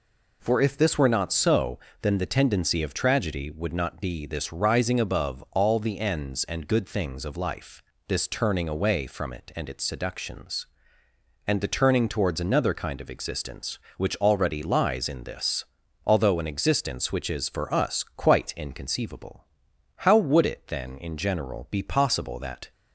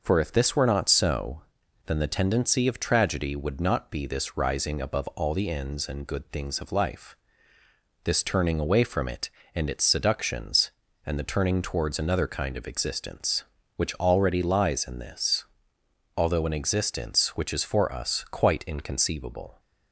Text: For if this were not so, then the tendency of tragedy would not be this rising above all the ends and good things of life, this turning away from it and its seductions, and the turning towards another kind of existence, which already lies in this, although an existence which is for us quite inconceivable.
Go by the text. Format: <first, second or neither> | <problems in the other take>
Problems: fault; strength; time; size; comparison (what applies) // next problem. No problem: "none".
second | goes on to say "How would it then in general be possible that"; strong; from 19.9 s on; 2.7 s long